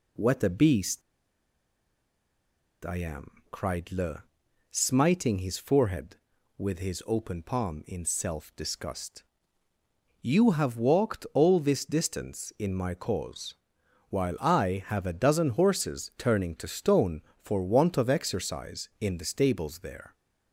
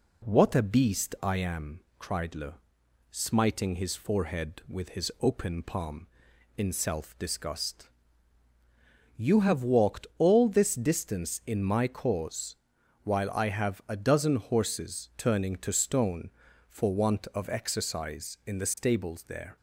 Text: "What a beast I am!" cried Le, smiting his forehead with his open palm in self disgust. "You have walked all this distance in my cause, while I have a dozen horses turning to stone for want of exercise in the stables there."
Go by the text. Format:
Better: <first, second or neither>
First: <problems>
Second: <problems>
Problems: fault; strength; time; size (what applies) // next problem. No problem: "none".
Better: second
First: pauses between "beast" and "I"; strong; at 1.0 s; 1.8 s long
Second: none